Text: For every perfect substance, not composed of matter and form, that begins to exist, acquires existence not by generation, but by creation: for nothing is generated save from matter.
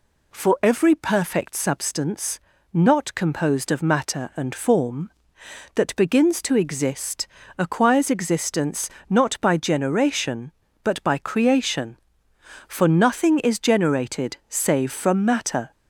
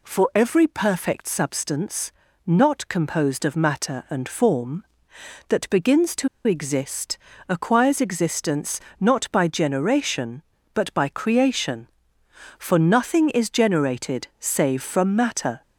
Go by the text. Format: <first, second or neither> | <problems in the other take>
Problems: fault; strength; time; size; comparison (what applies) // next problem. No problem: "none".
first | pauses between "to" and "exist"; slight; at 6.2 s; 0.19 s long // pauses between "existence" and "not"; slight; at 8.7 s; 0.20 s long; slight in the first